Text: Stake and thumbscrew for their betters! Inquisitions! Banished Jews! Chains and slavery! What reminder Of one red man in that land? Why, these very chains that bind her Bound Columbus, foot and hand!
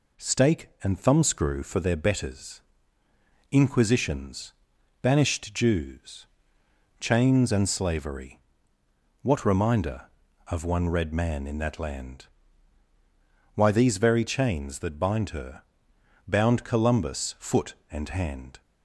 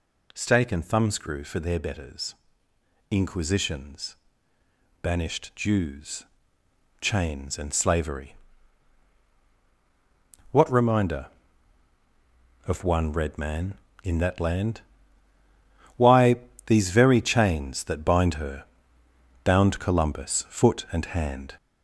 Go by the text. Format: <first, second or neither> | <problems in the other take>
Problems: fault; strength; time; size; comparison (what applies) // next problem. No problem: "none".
first | gets louder; noticeable; throughout; 5 dB // pauses between "her" and "Bound"; noticeable; at 18.6 s; 0.80 s long; noticeable in the first